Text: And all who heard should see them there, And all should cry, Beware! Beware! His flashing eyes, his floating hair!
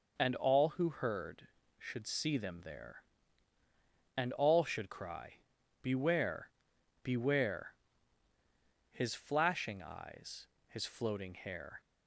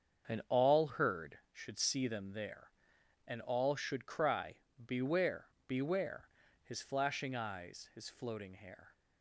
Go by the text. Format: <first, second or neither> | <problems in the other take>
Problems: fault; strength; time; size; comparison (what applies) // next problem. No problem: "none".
first | starts louder than the rest; until 1.3 s; 7 dB // skips "who"; at 0.8 s